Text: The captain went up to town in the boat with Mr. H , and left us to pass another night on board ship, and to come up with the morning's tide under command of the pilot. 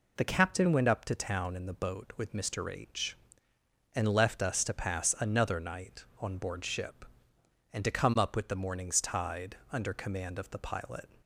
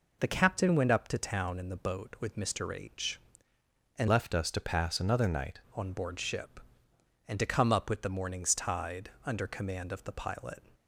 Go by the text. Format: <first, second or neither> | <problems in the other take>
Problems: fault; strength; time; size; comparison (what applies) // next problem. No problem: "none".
first | changes voice from "left" to "night"; from 4.0 to 5.5 s; 1.5 s long